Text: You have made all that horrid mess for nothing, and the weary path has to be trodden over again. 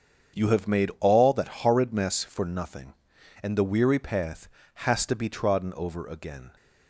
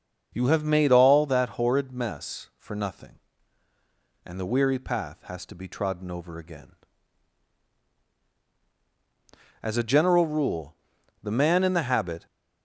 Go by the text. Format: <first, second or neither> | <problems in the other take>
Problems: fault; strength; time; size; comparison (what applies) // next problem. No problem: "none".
first | starts louder than the rest; until 1.3 s; 6 dB; strong in the first // goes on to say "As a general rule the man in the habit"; strong; from 9.6 s on; 2.6 s long